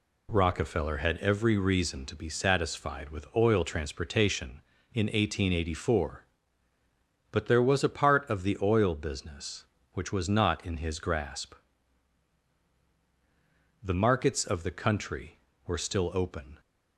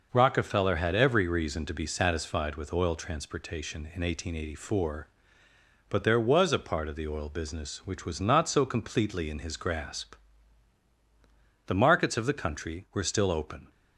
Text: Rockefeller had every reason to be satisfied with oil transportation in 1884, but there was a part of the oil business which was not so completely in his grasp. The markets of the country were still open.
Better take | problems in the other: second | skips "so completely"; at 10.6 s

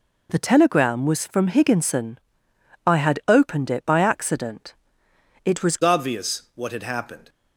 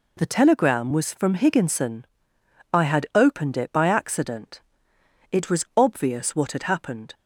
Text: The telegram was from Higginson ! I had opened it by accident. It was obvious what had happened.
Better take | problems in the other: second | changes voice at "obvious"; from 5.8 s on; 1.4 s long

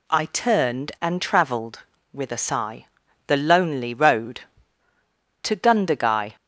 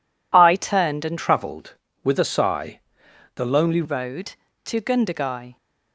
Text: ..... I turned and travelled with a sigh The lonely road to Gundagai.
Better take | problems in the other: first | changes voice from "travelled" to "lonely"; from 1.1 to 3.8 s; 2.7 s long // pauses between "sigh" and "The"; noticeable; at 2.7 s; 0.56 s long; also in the first

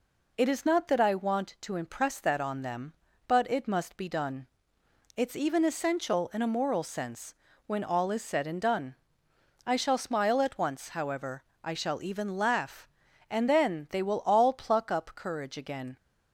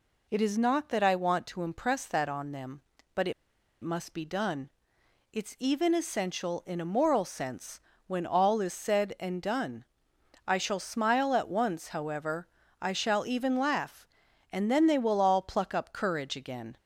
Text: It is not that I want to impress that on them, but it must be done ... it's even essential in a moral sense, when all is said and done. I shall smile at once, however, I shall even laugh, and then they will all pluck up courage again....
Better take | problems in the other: first | pauses between "it" and "must"; noticeable; at 3.3 s; 0.51 s long

